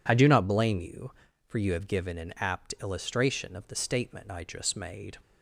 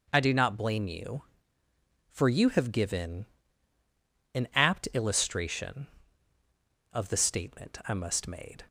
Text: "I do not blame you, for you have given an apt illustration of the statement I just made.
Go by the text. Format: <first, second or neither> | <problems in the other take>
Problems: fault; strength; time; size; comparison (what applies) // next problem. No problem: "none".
first | pauses between "given" and "an"; at 3.2 s; 1.0 s long // says "must" for "just"; at 7.9 s